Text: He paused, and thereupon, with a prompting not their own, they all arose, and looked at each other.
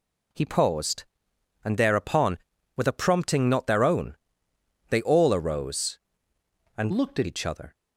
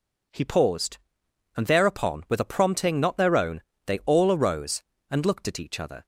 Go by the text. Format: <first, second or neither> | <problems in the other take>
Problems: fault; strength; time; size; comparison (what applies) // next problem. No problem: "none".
second | changes voice from "looked" to "at"; from 6.8 to 7.2 s; 0.4 s long